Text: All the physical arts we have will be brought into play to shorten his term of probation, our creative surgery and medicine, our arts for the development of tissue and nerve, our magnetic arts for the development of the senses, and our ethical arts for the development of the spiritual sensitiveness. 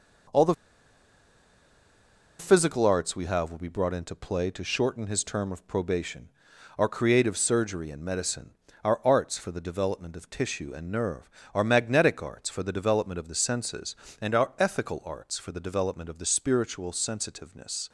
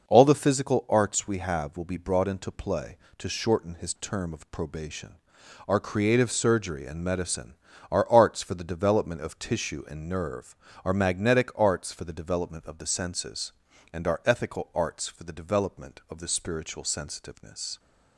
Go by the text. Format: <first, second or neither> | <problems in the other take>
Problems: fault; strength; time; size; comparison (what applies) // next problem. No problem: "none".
second | pauses between "the" and "physical"; strong; at 0.5 s; 1.8 s long